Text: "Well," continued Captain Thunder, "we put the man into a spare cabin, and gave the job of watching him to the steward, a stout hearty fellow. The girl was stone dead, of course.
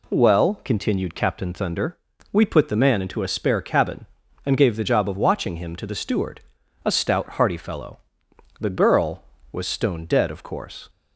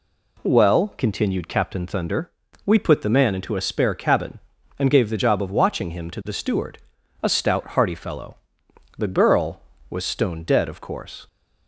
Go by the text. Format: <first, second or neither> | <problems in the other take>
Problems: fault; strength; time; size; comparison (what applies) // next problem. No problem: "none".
neither | none